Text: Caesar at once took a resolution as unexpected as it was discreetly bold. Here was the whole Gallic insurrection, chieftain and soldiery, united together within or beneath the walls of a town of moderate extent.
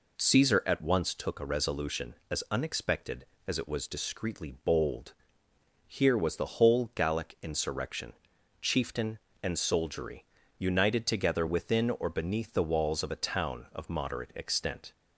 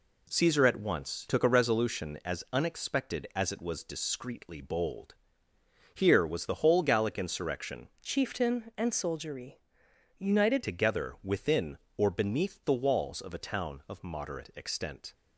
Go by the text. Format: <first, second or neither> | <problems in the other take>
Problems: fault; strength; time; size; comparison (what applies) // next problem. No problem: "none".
first | changes voice from "chieftain" to "united"; from 8.0 to 10.6 s; 2.6 s long